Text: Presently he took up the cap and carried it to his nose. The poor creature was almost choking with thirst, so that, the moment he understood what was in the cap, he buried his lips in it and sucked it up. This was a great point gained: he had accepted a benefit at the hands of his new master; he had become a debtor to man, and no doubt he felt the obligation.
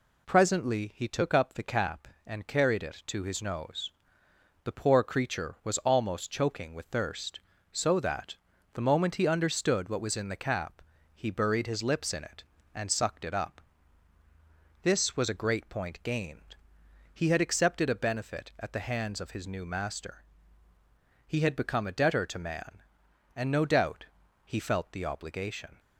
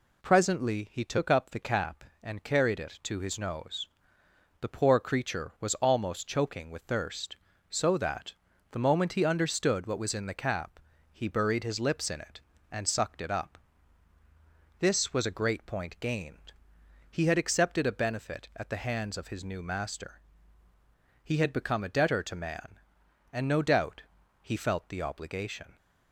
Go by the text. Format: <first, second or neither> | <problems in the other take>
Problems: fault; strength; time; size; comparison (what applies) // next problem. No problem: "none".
neither | pauses between "doubt" and "he"; the same in both